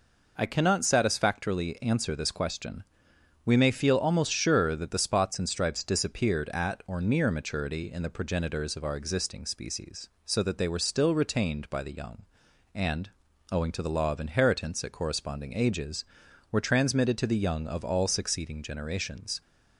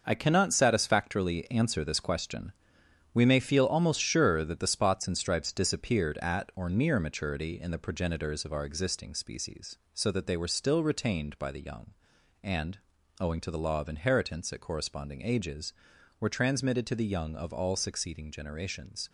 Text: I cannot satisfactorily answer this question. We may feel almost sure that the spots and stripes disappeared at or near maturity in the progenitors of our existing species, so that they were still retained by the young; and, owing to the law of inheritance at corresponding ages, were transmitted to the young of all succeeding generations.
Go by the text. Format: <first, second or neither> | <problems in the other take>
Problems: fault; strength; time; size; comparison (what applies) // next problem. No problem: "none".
first | gets quieter; strong; throughout; 8.5 dB